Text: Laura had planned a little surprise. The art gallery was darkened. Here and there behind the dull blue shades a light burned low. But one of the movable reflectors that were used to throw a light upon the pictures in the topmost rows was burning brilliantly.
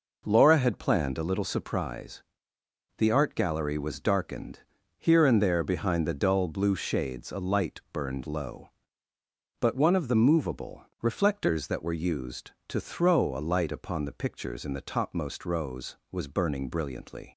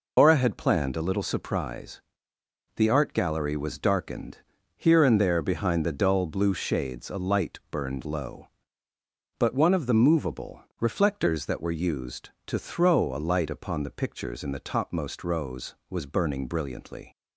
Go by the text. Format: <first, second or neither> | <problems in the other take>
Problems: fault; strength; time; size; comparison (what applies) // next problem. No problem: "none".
first | loses the start of "Laura"; at 0.1 s; 150 ms // pauses between "movable" and "reflectors"; slight; at 10.6 s; 0.16 s long; slight in the first